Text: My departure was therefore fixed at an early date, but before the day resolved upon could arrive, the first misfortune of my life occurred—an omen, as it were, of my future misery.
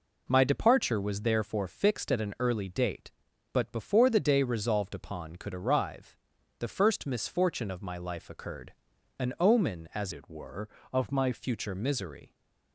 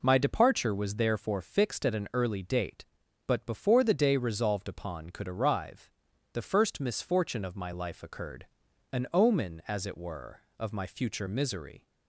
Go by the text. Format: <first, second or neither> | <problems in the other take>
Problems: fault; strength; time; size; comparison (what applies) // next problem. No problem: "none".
second | changes voice from "it" to "my"; from 10.1 to 11.3 s; 1.2 s long